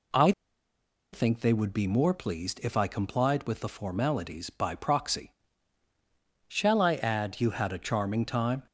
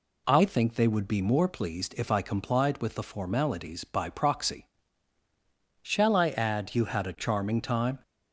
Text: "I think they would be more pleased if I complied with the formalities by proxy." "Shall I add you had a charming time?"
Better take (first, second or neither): second